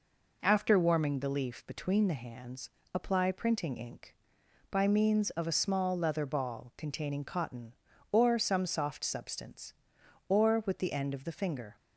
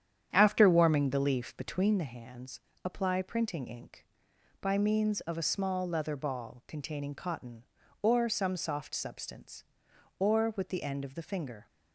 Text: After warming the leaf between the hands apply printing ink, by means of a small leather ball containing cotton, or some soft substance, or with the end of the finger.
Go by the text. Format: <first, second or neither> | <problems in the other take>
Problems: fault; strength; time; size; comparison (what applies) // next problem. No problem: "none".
first | starts louder than the rest; strong; until 2.0 s; 9 dB // pauses between "hands" and "apply"; slight; at 2.6 s; 0.24 s long; slight in the first